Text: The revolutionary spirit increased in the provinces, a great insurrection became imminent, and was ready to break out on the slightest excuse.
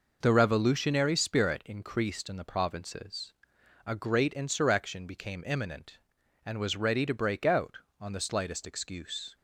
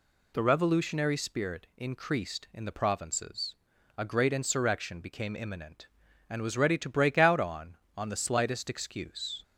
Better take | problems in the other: first | says "on" twice; at 7.9 s

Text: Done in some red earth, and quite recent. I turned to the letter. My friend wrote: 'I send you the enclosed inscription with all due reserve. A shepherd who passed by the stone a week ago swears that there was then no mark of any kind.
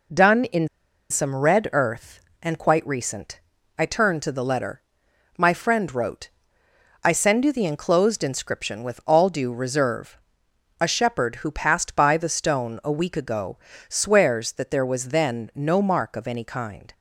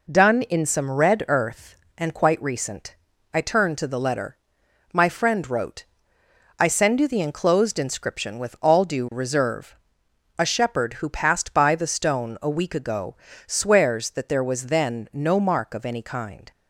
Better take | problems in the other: second | pauses between "in" and "some"; at 0.6 s; 0.43 s long // pauses between "ago" and "swears"; slight; at 13.5 s; 0.32 s long; slight in the second

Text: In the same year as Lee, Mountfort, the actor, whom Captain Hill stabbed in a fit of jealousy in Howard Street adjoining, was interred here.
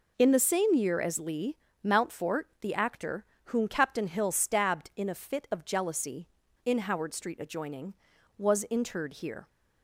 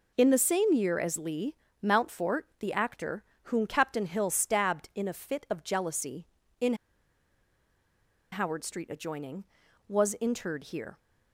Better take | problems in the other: first | pauses between "in" and "Howard"; strong; at 6.7 s; 1.5 s long

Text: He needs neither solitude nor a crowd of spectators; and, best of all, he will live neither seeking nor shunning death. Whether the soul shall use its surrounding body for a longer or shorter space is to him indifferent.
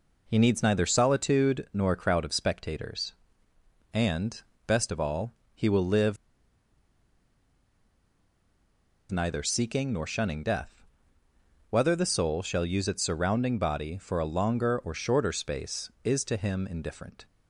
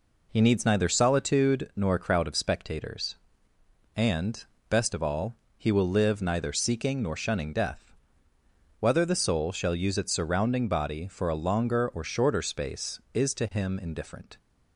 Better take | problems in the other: second | pauses between "live" and "neither"; strong; at 6.1 s; 2.9 s long

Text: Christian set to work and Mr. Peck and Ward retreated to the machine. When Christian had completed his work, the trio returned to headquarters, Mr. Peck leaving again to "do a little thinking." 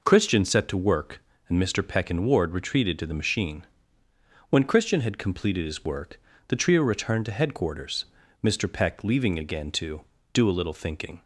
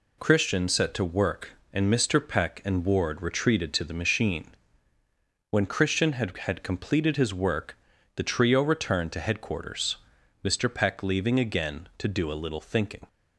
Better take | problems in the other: first | says "had" twice; at 6.3 s

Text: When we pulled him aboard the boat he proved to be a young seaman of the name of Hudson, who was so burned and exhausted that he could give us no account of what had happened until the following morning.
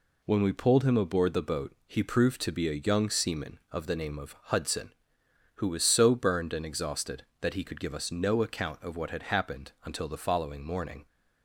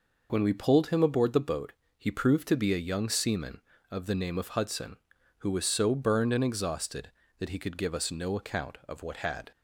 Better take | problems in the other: first | pauses between "boat" and "he"; slight; at 1.7 s; 0.26 s long // stops before "happened until the following morning"; at 9.5 s

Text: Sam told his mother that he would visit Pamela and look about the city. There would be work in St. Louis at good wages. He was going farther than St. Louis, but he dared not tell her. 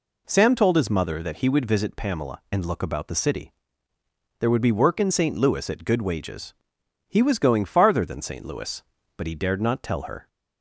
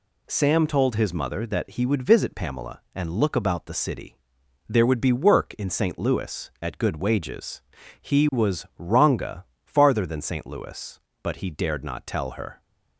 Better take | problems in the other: first | says "ranga" for "going"; at 8.7 s

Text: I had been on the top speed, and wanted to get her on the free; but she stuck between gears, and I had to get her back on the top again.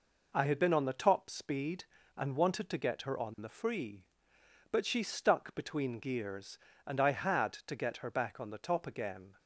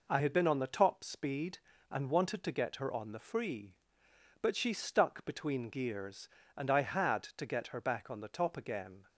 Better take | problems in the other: neither | none

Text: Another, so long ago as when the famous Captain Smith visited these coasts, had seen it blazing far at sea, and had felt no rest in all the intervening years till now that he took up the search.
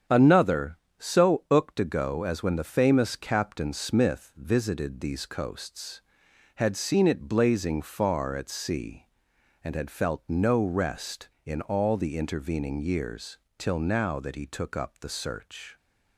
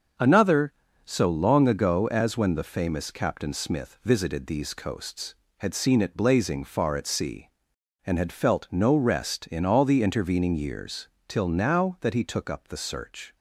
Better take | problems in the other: second | starts louder than the rest; strong; until 1.3 s; 8.5 dB; also in the second // says "ooked" for "long"; at 1.4 s // pauses between "years" and "till"; slight; at 13.3 s; 0.20 s long; slight in the second

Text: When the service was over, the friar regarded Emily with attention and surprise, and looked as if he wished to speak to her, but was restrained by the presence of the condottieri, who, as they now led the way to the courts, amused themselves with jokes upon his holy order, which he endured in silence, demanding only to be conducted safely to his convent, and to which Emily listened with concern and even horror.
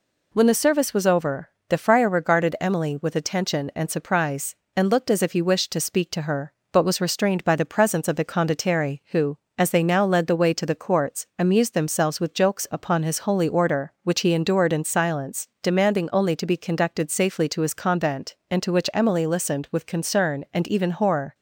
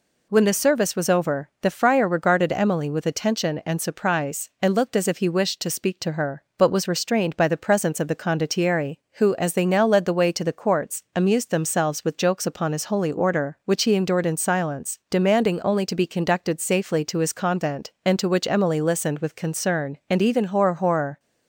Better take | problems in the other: first | says "horror" twice; at 20.7 s

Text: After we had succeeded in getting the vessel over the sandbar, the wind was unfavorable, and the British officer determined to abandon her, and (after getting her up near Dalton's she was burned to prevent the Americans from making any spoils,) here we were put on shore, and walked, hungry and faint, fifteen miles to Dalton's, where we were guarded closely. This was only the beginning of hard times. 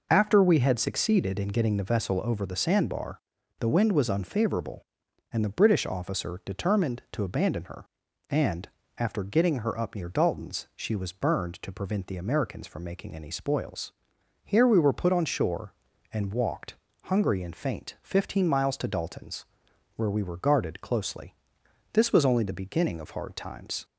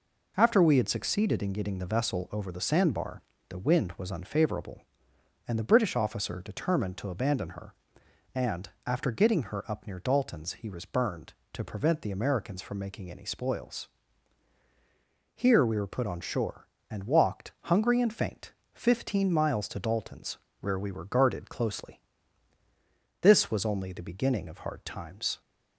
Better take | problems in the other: first | says "he" for "she"; at 10.5 s

